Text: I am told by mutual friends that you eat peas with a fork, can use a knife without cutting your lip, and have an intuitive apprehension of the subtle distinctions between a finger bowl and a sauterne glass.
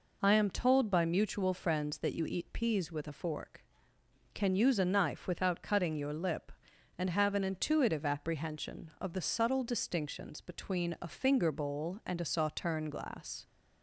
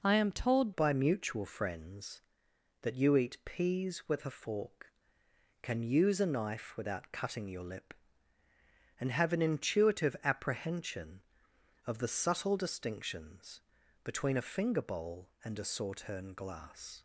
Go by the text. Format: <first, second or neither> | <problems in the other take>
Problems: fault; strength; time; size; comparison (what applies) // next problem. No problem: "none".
first | changes voice at "by"; from 0.7 s on; 16.3 s long // pauses between "distinctions" and "between"; at 13.5 s; 0.44 s long